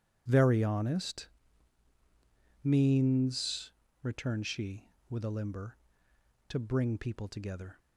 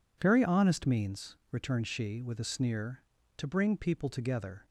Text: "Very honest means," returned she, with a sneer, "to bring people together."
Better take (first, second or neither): second